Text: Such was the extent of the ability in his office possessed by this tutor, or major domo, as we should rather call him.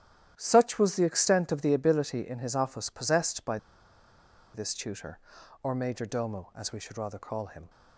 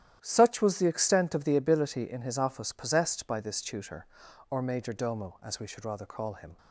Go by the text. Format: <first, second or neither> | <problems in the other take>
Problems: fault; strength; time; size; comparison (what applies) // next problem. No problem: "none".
second | starts louder than the rest; strong; until 1.3 s; 11.5 dB; strong in the second // pauses between "by" and "this"; noticeable; at 3.5 s; 0.97 s long